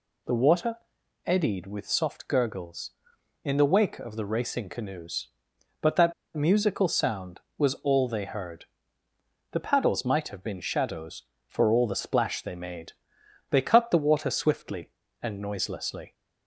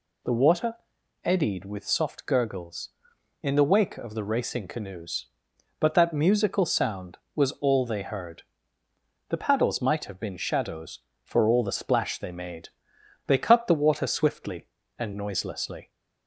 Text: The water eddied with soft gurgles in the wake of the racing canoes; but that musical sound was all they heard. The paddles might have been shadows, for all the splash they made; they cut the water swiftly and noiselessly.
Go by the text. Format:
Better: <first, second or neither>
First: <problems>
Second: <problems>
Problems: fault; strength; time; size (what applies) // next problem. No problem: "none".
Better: second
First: pauses between "water" and "eddied"; noticeable; at 0.7 s; 0.48 s long // pauses between "that" and "musical"; slight; at 6.1 s; 0.21 s long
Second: pauses between "water" and "eddied"; noticeable; at 0.7 s; 0.48 s long